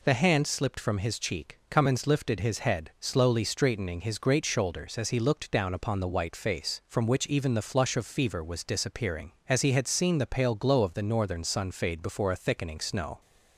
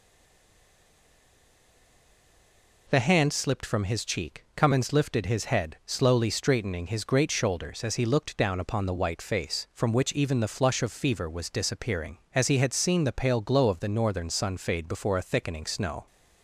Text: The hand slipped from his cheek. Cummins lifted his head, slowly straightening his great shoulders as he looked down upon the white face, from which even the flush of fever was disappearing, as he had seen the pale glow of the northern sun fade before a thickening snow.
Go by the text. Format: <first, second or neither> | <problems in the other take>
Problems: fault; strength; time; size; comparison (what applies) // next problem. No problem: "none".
first | stays silent before the first word; strong; until 2.8 s; 2.8 s long